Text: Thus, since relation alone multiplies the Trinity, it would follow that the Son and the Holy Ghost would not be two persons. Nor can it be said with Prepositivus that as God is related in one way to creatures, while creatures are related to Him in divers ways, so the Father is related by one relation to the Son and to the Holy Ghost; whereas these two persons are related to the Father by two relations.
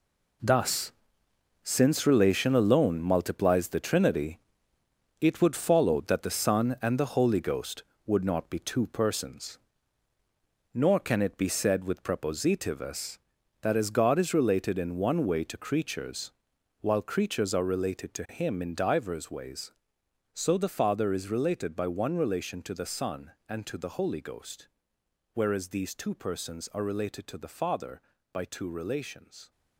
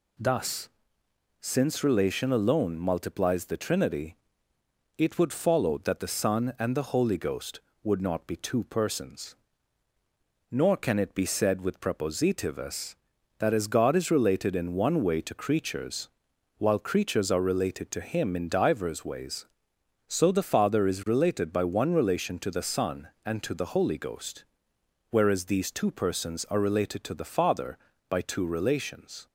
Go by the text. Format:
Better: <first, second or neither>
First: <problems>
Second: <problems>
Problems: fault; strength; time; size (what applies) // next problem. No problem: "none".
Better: second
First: gets quieter; strong; throughout; 10 dB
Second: none